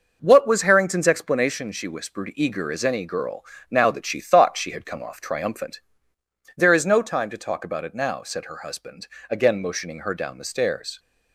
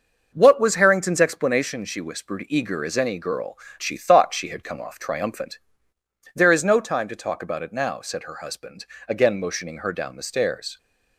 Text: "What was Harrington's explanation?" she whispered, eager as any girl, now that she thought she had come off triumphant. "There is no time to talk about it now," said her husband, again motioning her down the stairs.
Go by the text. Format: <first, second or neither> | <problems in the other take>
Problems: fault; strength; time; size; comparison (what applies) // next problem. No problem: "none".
first | starts louder than the rest; noticeable; until 1.3 s; 6 dB // skips "now that"; at 3.6 s